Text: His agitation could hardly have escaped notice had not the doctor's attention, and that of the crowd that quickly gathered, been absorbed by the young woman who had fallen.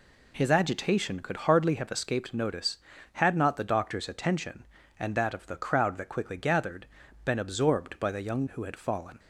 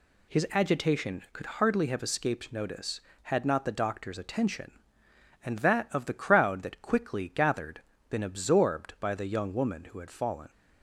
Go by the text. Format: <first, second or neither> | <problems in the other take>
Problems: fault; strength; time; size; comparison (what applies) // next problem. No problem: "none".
second | skips "woman"; at 8.4 s